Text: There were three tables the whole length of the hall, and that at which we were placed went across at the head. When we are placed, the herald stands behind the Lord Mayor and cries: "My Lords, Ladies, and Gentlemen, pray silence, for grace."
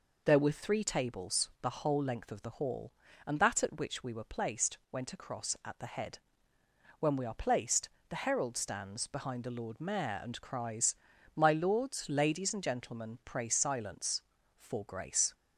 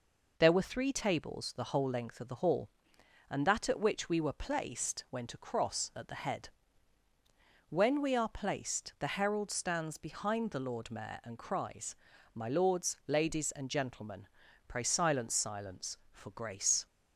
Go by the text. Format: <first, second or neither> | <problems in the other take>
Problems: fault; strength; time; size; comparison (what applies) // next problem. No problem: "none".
first | says "silence" twice; at 15.3 s